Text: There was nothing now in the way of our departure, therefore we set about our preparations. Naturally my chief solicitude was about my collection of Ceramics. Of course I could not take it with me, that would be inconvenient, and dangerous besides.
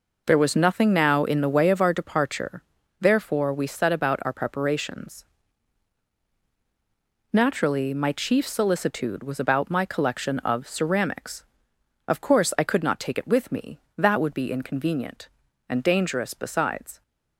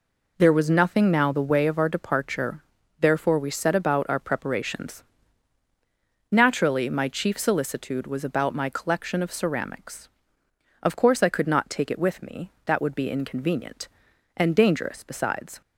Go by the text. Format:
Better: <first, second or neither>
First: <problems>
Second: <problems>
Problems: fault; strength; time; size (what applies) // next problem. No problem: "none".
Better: first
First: none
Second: skips "in"; at 1.3 s